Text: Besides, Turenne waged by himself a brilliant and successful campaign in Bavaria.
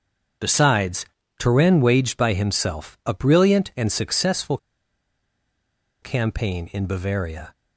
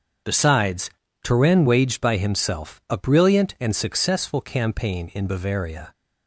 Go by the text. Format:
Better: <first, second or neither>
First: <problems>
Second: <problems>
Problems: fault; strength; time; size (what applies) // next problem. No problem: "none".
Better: second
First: starts louder than the rest; strong; until 1.7 s; 7 dB // pauses between "successful" and "campaign"; strong; at 4.5 s; 1.4 s long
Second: starts louder than the rest; strong; until 1.6 s; 7 dB